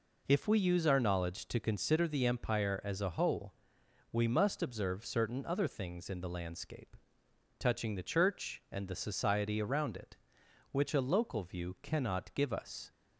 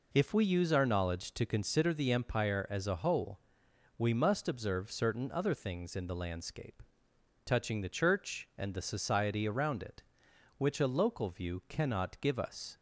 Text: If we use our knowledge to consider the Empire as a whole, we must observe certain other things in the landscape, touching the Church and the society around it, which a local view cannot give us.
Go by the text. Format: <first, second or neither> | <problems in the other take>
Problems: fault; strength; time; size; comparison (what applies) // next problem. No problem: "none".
neither | none